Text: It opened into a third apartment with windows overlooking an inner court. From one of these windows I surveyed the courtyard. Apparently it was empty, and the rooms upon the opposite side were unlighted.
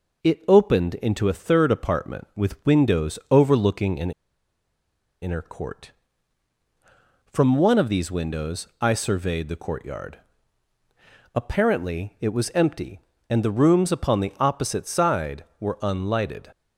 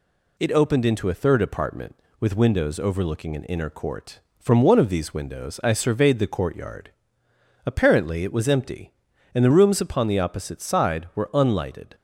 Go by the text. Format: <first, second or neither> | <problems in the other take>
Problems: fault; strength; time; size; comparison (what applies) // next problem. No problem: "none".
second | pauses between "an" and "inner"; at 4.1 s; 1.1 s long // pauses between "windows" and "I"; slight; at 8.6 s; 0.16 s long